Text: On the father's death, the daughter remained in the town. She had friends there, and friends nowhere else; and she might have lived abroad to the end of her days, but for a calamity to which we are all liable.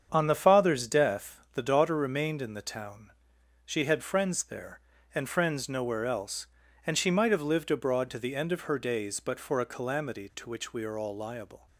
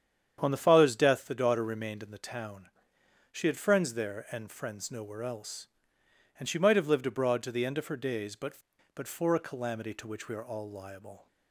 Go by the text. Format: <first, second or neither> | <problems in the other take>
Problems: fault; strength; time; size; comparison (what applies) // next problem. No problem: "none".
first | starts louder than the rest; strong; until 1.4 s; 8.5 dB; strong in the first // says "but" twice; at 8.9 s